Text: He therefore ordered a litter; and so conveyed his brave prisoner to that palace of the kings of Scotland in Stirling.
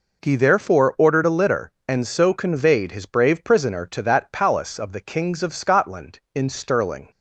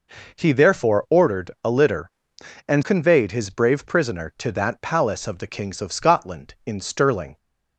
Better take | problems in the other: first | skips "so"; at 2.8 s

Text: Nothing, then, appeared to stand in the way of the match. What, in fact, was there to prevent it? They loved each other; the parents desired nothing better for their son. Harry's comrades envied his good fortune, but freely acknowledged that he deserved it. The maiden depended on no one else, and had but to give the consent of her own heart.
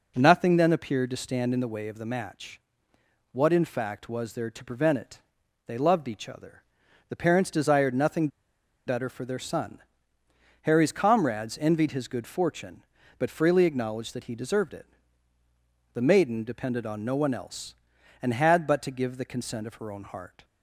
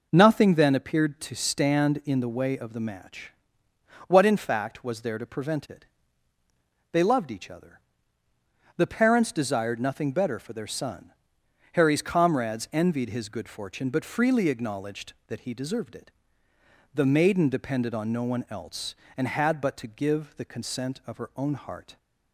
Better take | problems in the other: second | pauses between "nothing" and "better"; noticeable; at 8.2 s; 0.59 s long

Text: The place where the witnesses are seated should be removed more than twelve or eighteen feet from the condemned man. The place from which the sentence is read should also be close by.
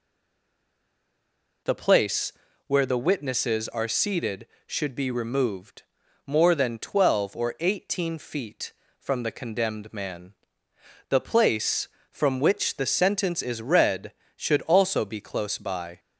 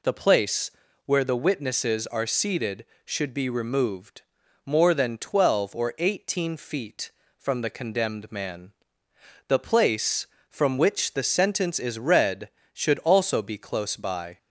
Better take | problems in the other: second | stays silent before the first word; noticeable; until 1.6 s; 1.6 s long // pauses between "place" and "where"; slight; at 2.3 s; 0.32 s long; slight in the second // pauses between "removed" and "more"; at 5.8 s; 0.42 s long; also in the second

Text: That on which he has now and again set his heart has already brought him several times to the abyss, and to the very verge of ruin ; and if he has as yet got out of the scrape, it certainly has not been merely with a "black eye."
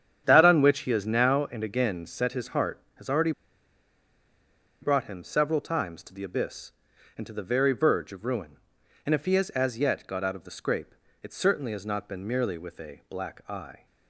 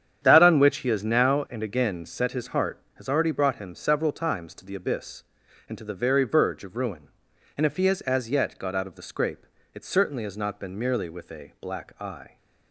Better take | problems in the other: second | starts louder than the rest; strong; until 1.2 s; 9 dB; strong in the second // pauses between "already" and "brought"; strong; at 3.3 s; 1.5 s long

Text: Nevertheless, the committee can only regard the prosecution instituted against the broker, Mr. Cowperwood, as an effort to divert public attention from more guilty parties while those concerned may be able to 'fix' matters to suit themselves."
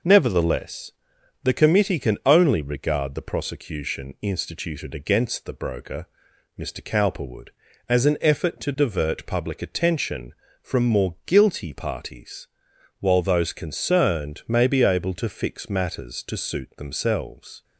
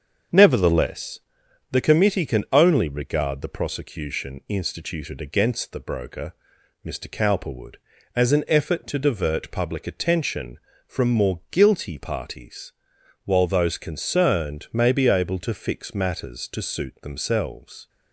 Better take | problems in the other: first | starts louder than the rest; until 1.4 s; 7 dB // pauses between "parties" and "while"; noticeable; at 12.7 s; 0.52 s long; noticeable in the first

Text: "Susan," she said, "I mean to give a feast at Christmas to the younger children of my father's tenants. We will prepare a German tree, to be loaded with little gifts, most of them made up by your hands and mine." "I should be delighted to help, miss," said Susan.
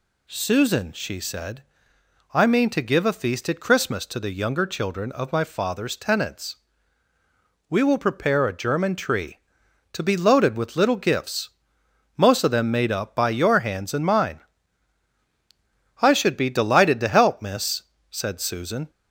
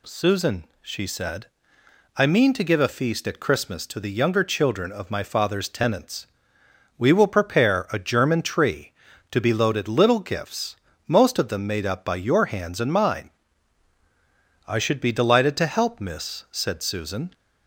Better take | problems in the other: first | skips "with"; at 9.8 s

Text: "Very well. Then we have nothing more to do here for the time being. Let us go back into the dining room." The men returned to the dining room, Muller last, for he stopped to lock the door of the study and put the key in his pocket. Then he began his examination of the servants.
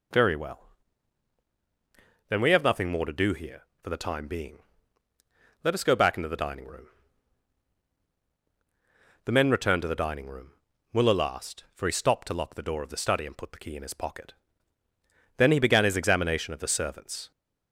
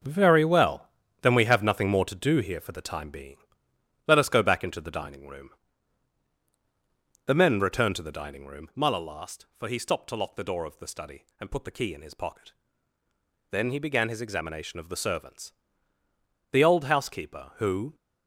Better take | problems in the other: first | goes on to say "The old housekeeper who"; from 16.5 s on; 1.4 s long

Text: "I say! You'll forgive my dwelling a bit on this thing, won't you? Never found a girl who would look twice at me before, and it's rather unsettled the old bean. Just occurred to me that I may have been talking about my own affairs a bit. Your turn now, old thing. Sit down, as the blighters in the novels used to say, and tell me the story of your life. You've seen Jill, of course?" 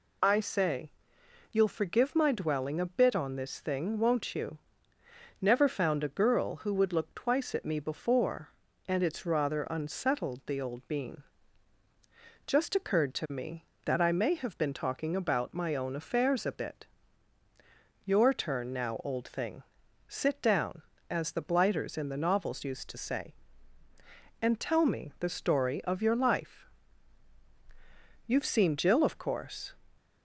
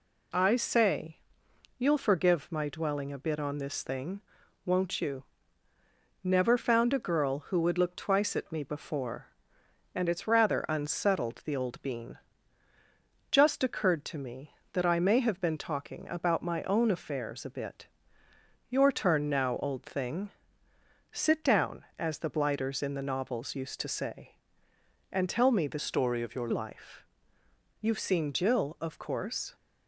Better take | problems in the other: first | changes voice from "story" to "your"; from 25.7 to 26.4 s; 0.7 s long

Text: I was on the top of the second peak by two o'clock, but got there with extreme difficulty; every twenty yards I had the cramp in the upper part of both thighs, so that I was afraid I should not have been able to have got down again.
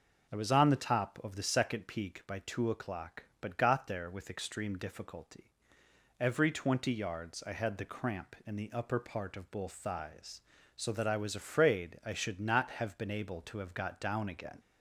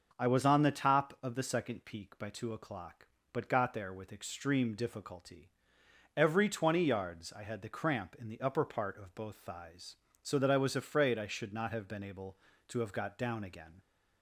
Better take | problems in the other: neither | none

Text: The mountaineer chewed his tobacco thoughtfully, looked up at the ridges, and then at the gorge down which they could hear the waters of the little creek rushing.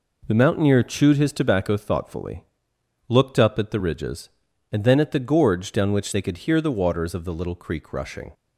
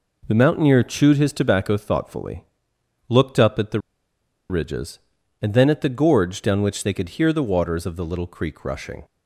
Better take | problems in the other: first | pauses between "the" and "ridges"; noticeable; at 3.7 s; 0.69 s long

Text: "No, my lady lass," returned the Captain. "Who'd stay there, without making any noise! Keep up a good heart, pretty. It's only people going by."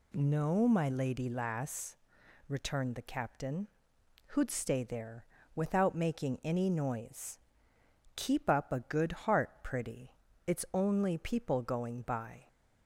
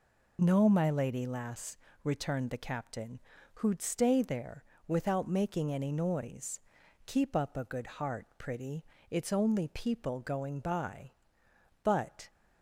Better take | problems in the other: first | goes on to say "But"; slight; from 11.8 s on; 0.46 s long

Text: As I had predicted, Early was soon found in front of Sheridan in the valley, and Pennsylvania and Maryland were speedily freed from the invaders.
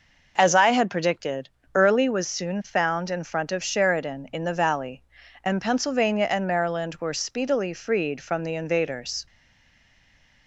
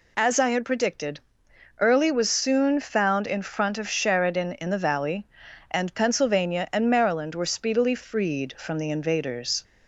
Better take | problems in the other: second | stays silent after the last word; noticeable; from 9.2 s on; 1.2 s long

